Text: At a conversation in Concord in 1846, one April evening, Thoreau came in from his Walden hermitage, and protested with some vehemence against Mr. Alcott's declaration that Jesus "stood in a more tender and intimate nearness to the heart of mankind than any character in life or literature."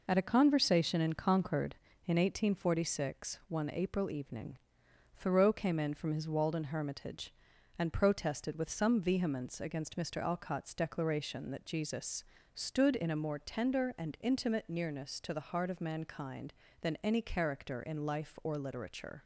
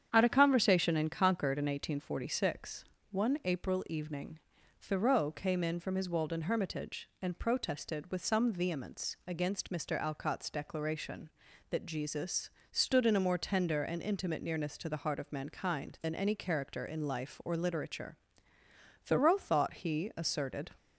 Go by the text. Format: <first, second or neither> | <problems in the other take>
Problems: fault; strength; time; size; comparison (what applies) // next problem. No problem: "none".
first | starts louder than the rest; strong; until 1.1 s; 8.5 dB // pauses between "Jesus" and "stood"; slight; at 12.4 s; 0.22 s long; slight in the first // goes on to say "Thoreau thought he asserted"; strong; from 19.0 s on; 1.6 s long